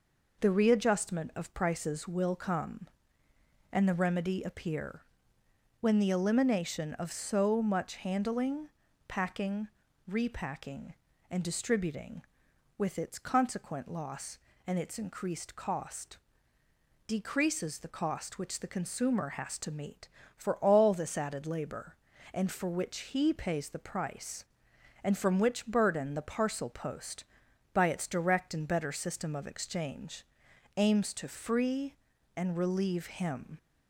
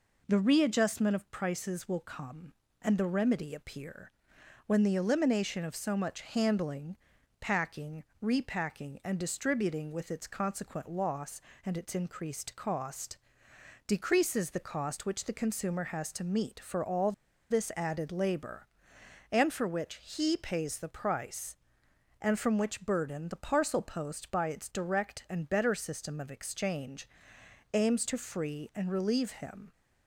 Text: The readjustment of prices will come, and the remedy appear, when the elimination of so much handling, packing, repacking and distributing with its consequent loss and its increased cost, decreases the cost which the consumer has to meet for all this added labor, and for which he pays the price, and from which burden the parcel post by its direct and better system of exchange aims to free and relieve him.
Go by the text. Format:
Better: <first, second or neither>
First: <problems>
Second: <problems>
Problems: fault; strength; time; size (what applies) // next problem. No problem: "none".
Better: first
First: pauses between "exchange" and "aims"; noticeable; at 30.2 s; 0.54 s long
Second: pauses between "all" and "this"; at 17.1 s; 0.38 s long // pauses between "exchange" and "aims"; noticeable; at 27.0 s; 0.64 s long